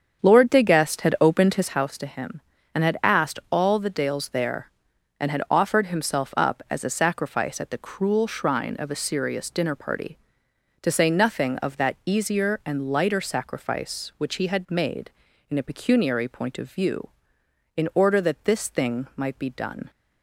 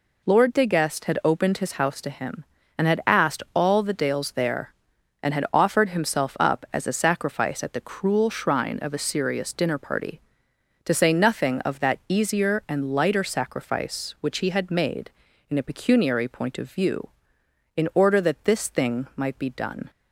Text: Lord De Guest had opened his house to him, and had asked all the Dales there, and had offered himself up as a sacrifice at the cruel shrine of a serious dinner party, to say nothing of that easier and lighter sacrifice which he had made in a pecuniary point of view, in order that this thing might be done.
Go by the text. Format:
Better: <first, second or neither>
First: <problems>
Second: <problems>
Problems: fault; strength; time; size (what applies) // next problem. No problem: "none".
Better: second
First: starts louder than the rest; strong; until 1.8 s; 7.5 dB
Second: none